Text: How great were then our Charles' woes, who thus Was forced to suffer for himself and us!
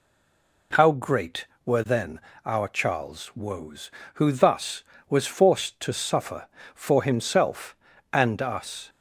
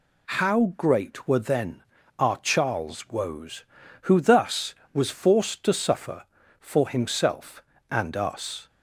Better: second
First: stays silent before the first word; slight; until 0.7 s; 0.7 s long // pauses between "then" and "our"; slight; at 2.1 s; 0.28 s long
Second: pauses between "then" and "our"; slight; at 1.8 s; 0.34 s long

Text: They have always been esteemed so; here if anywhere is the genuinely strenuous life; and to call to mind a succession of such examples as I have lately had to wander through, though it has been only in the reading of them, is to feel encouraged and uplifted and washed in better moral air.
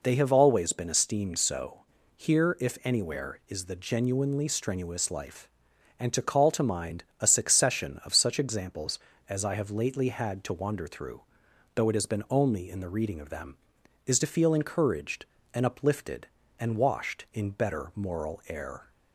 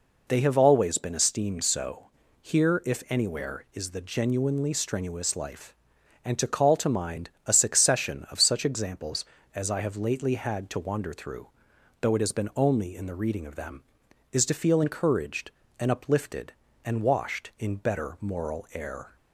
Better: neither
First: pauses between "mind" and "a"; slight; at 7.0 s; 0.16 s long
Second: pauses between "mind" and "a"; slight; at 7.2 s; 0.16 s long

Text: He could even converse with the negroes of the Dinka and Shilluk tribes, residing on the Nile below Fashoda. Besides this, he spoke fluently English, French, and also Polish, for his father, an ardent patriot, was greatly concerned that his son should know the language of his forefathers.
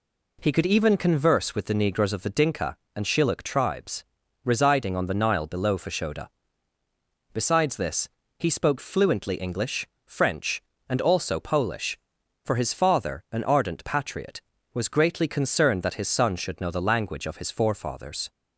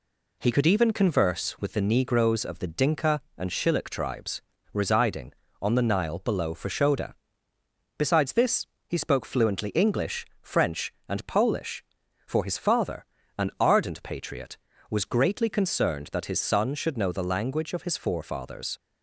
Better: first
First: none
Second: skips "also"; at 11.2 s

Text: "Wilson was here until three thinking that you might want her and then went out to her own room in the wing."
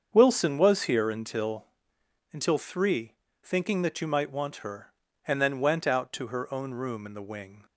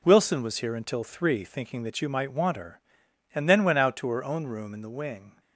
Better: second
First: starts louder than the rest; until 1.1 s; 7 dB // says "until" twice; at 2.3 s // pauses between "three" and "thinking"; slight; at 3.1 s; 0.26 s long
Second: none

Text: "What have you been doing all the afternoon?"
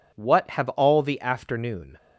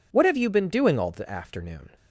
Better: second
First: skips "you been doing"; at 0.6 s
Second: none

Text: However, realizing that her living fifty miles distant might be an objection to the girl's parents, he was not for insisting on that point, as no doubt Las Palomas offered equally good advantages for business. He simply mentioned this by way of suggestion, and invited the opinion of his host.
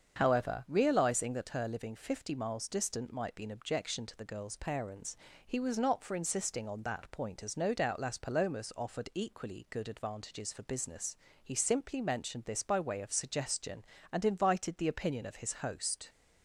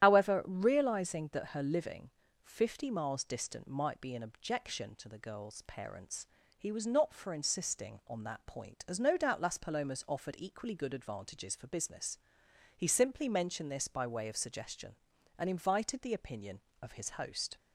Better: first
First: starts louder than the rest; until 1.1 s; 7 dB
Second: loses the start of "However"; at 0.0 s; 80 ms // starts louder than the rest; strong; until 1.0 s; 11.5 dB // pauses between "living" and "fifty"; slight; at 2.1 s; 0.34 s long

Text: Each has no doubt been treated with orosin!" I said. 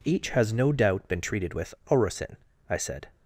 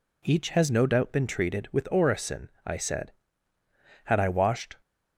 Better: first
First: none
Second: goes on to say "Had I washed"; noticeable; from 4.0 s on; 0.72 s long

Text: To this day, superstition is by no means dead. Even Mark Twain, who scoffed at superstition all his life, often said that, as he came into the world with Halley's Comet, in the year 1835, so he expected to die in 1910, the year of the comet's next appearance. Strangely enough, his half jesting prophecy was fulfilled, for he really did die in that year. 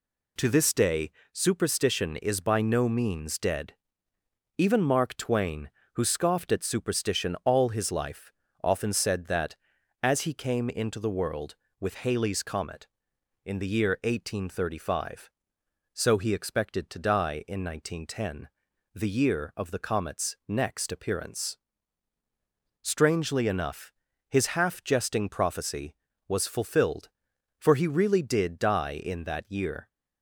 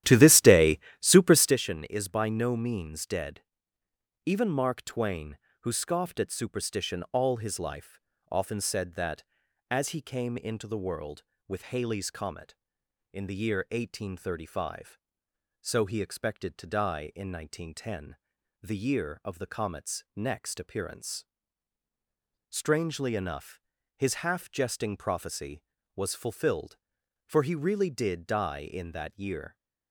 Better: first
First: none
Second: starts louder than the rest; strong; until 1.6 s; 12.5 dB

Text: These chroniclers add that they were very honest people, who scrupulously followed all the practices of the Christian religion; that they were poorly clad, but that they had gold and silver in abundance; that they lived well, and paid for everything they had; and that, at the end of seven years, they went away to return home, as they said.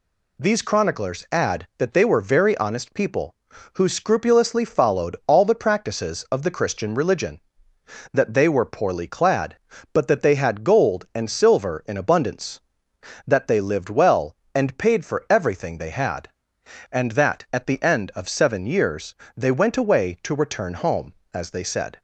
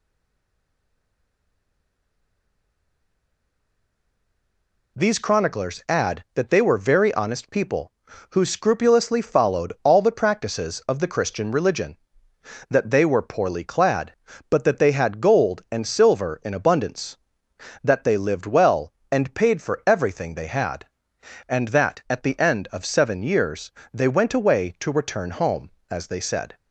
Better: first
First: none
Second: stays silent before the first word; strong; until 4.9 s; 4.9 s long

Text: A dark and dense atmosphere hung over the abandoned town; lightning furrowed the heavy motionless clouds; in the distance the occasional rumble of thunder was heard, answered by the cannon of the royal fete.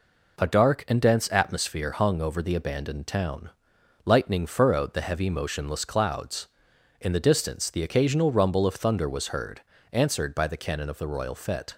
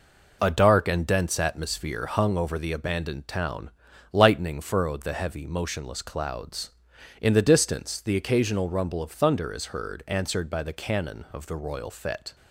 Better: first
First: none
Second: says "is" for "was"; at 9.5 s

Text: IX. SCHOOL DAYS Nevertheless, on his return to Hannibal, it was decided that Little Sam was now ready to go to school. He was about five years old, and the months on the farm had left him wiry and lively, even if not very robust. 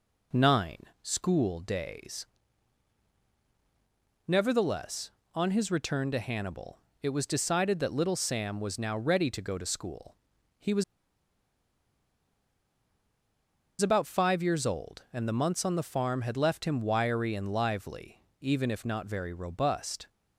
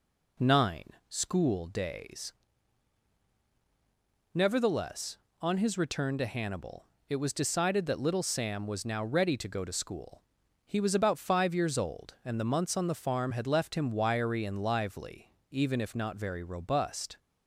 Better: second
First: pauses between "DAYS" and "Nevertheless"; strong; at 2.2 s; 2.0 s long // pauses between "was" and "about"; strong; at 10.8 s; 2.9 s long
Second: pauses between "DAYS" and "Nevertheless"; strong; at 2.3 s; 2.0 s long

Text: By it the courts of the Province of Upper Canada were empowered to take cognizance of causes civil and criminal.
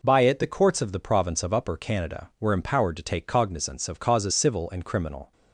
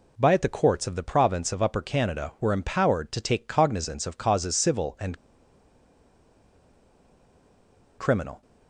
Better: first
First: none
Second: pauses between "and" and "criminal"; strong; at 5.1 s; 2.8 s long

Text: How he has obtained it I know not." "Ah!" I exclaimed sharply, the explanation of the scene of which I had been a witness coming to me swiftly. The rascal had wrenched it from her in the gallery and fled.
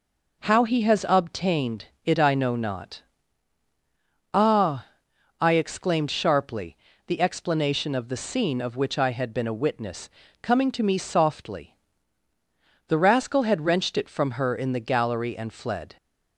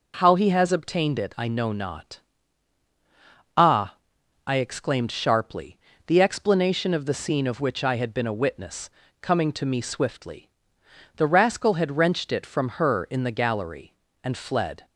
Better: second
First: pauses between "obtained" and "it"; slight; at 1.8 s; 0.18 s long // pauses between "witness" and "coming"; slight; at 10.0 s; 0.32 s long // says "softly" for "swiftly"; at 10.9 s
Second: pauses between "witness" and "coming"; slight; at 8.8 s; 0.32 s long

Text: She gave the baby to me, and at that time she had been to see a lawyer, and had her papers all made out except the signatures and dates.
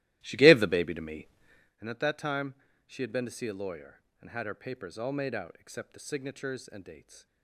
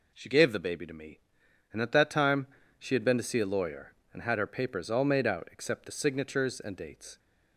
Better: second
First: starts louder than the rest; strong; until 1.8 s; 15.5 dB // pauses between "time" and "she"; slight; at 2.5 s; 0.32 s long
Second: pauses between "time" and "she"; slight; at 2.4 s; 0.32 s long

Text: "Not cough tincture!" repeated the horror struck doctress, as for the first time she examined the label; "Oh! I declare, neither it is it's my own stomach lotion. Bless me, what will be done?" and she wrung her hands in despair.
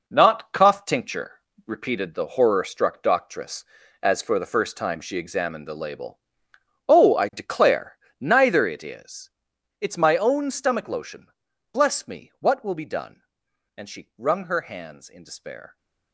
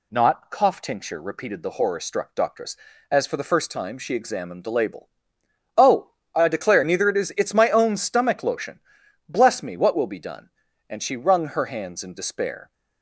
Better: second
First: gets quieter; strong; throughout; 8.5 dB // pauses between "is" and "it's"; noticeable; at 9.3 s; 0.50 s long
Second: none

